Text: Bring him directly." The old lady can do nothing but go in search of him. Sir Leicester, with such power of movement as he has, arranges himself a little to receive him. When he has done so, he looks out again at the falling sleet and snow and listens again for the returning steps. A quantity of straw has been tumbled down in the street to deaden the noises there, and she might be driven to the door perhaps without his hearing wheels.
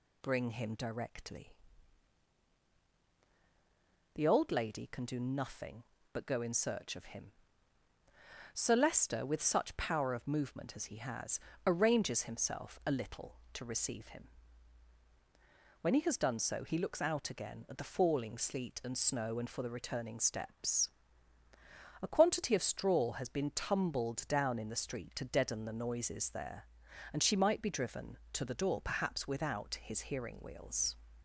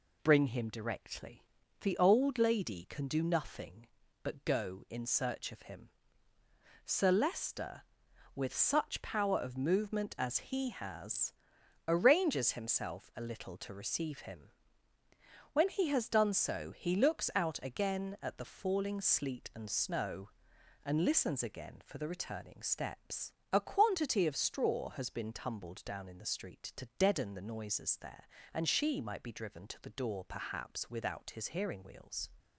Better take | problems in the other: second | skips "listens again"; at 19.4 s

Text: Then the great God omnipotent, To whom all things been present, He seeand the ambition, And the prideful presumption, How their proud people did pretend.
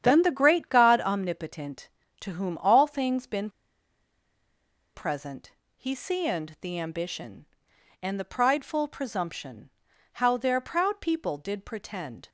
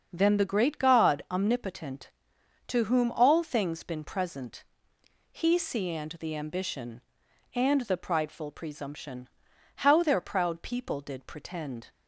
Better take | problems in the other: second | starts louder than the rest; strong; until 1.0 s; 9 dB; also in the second // pauses between "been" and "present"; strong; at 3.4 s; 1.4 s long

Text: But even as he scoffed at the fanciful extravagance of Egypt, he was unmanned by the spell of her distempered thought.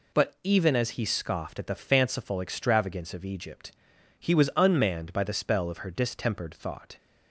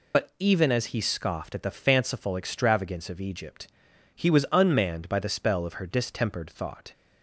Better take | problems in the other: first | loses the start of "But"; at 0.1 s; 45 ms

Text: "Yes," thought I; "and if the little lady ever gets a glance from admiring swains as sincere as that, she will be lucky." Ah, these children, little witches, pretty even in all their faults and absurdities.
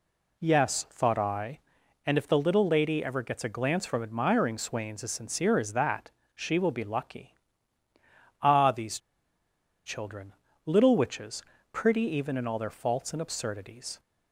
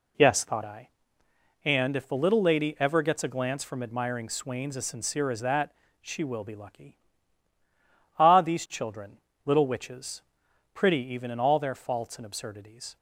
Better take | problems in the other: second | pauses between "these" and "children"; noticeable; at 8.9 s; 0.87 s long

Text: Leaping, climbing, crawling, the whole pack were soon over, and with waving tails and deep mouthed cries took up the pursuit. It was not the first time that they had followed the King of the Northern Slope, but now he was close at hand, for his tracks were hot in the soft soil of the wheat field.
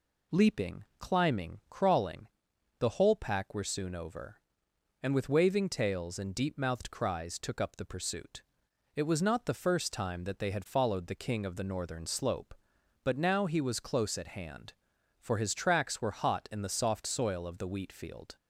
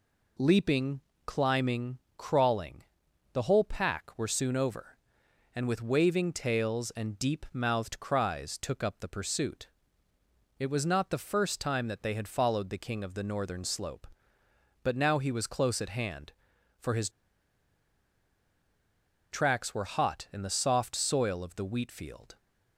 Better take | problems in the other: first | pauses between "his" and "tracks"; strong; at 17.0 s; 2.2 s long

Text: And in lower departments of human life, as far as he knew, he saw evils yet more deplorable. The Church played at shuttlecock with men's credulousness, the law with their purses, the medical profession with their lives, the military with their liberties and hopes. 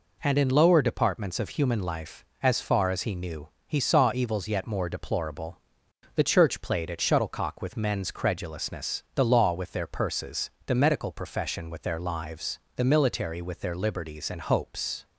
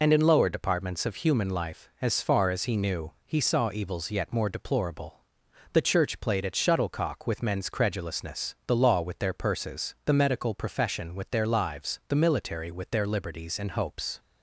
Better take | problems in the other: first | loses the start of "And"; at 0.0 s; 55 ms

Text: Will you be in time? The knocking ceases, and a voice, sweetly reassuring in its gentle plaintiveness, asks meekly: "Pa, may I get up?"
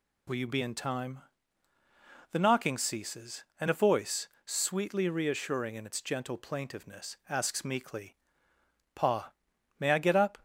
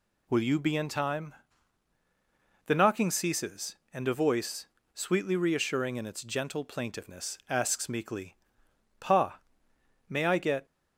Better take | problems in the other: first | stops before "up"; at 10.6 s

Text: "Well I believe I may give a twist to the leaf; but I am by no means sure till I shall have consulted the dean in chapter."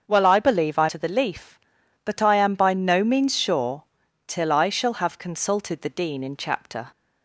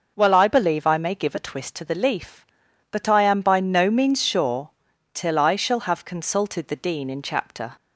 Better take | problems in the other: second | starts louder than the rest; until 1.0 s; 7 dB // skips "may give a twist"; at 0.8 s // pauses between "sure" and "till"; at 3.8 s; 0.44 s long; also in the second

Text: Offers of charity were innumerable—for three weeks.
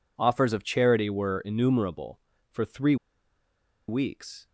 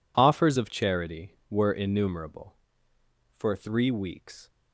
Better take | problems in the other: second | pauses between "three" and "weeks"; noticeable; at 2.9 s; 0.93 s long

